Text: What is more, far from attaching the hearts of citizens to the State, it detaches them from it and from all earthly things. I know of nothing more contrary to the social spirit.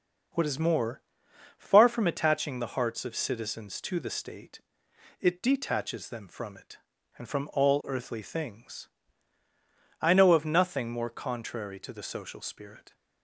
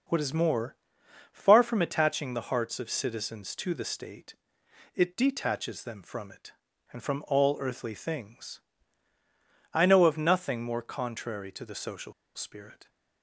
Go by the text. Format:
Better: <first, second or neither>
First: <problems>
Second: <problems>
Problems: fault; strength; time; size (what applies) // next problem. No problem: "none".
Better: first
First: none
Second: pauses between "social" and "spirit"; slight; at 12.1 s; 0.22 s long